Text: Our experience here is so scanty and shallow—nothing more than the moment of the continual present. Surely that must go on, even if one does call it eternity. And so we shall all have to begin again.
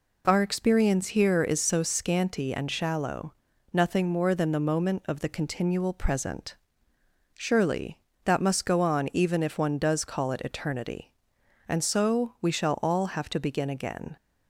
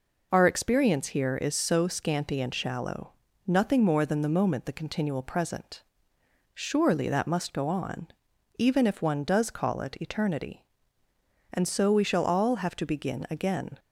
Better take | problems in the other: first | skips "of"; at 4.6 s

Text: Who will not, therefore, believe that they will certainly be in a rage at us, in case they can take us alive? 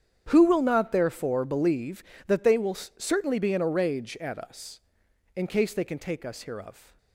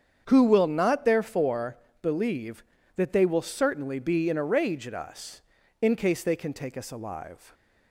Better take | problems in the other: second | starts louder than the rest; strong; until 1.2 s; 8.5 dB; strong in the second // says "hereof" for "alive"; at 6.4 s

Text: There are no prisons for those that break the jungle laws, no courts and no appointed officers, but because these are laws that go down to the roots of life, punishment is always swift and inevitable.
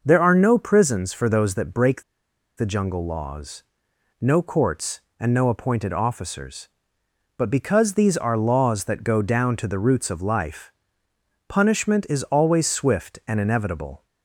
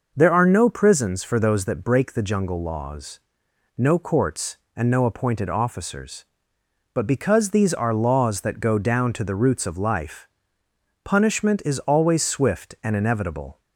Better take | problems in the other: second | pauses between "break" and "the"; noticeable; at 2.0 s; 0.55 s long

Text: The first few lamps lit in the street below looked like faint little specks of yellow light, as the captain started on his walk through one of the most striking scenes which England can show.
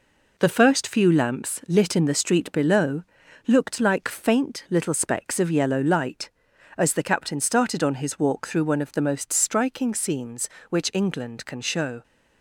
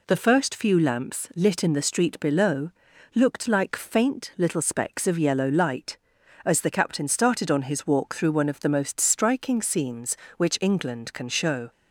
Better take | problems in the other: second | gets quieter; throughout; 6 dB // pauses between "below" and "looked"; at 3.0 s; 0.44 s long; also in the second

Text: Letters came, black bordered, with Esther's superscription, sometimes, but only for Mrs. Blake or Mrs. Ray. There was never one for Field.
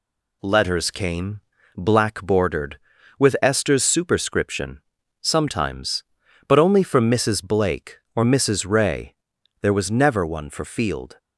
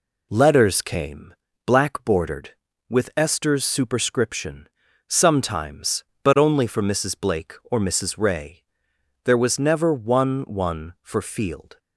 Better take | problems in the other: first | says "one" twice; at 10.4 s

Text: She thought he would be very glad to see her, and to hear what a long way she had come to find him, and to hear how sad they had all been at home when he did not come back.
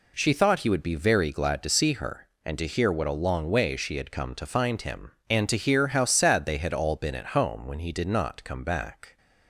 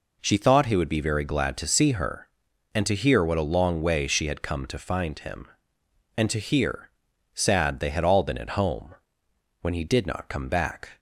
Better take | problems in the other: first | skips "how"; at 7.1 s // pauses between "home" and "when"; noticeable; at 8.9 s; 0.66 s long

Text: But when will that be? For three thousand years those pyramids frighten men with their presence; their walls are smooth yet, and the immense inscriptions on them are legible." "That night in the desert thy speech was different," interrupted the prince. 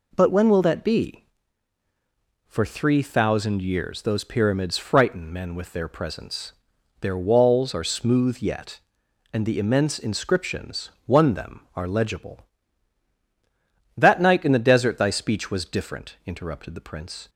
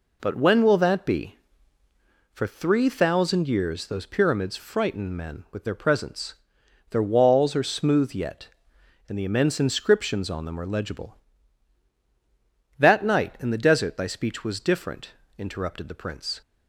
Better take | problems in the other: second | says "one" for "on"; at 11.0 s

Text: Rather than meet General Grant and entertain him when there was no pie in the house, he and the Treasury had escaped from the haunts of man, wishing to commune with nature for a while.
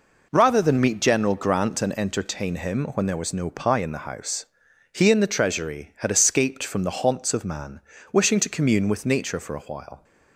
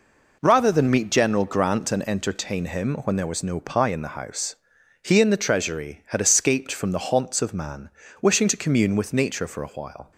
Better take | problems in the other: neither | none

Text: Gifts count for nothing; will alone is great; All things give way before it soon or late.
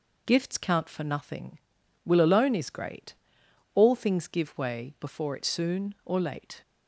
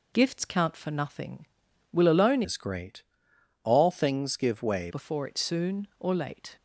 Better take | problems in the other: first | changes voice from "is" to "way"; from 2.4 to 4.8 s; 2.4 s long

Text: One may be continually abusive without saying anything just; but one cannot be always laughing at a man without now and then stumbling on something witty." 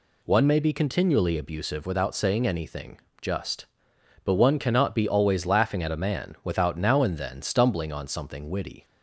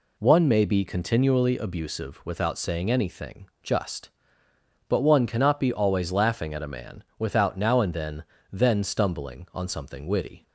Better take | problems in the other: first | pauses between "anything" and "just"; slight; at 3.4 s; 0.16 s long; slight in the first // pauses between "man" and "without"; slight; at 7.0 s; 0.16 s long // says "then" twice; at 8.4 s

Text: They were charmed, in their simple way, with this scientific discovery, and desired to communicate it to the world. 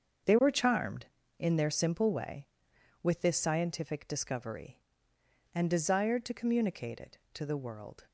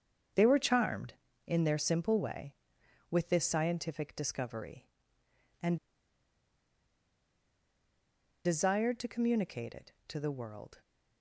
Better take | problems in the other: first | starts louder than the rest; until 1.6 s; 7 dB; also in the first // pauses between "and" and "desired"; strong; at 5.7 s; 2.6 s long

